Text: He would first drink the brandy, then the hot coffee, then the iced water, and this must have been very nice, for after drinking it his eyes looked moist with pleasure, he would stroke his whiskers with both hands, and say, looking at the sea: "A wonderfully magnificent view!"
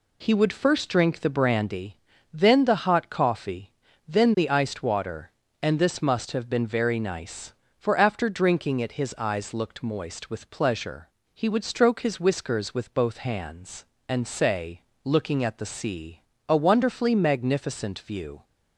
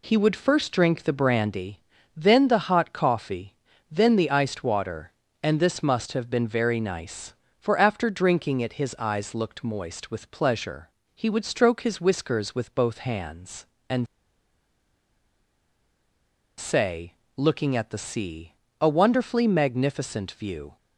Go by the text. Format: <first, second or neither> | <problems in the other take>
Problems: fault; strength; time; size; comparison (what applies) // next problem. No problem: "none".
first | pauses between "and" and "say"; strong; at 14.0 s; 2.5 s long